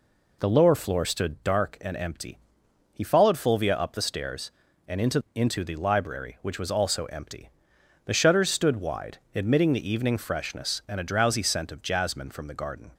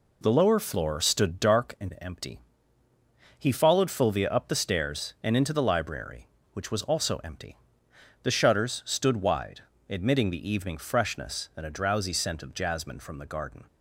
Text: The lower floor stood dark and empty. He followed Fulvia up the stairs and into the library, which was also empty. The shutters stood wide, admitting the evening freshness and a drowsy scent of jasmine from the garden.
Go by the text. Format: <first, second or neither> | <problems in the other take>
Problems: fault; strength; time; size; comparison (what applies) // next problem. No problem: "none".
second | says "into" twice; at 5.3 s